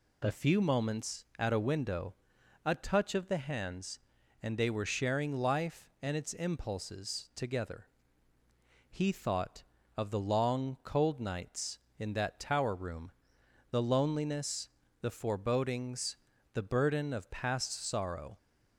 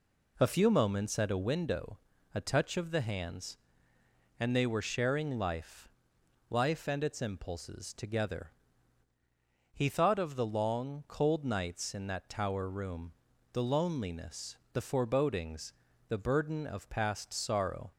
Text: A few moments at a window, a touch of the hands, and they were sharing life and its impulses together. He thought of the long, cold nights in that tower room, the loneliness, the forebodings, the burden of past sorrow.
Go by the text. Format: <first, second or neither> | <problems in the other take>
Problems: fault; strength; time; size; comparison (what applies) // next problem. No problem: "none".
first | says "life" twice; at 6.4 s